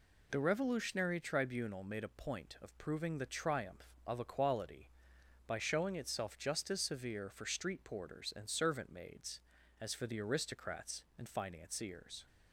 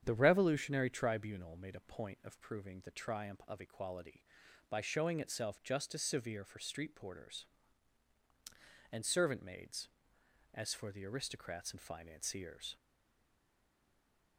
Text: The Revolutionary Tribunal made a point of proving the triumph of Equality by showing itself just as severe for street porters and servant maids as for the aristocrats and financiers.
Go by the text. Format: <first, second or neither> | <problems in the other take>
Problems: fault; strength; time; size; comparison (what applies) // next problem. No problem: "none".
first | starts louder than the rest; strong; until 1.0 s; 8.5 dB // stays silent after the last word; noticeable; from 12.7 s on; 1.6 s long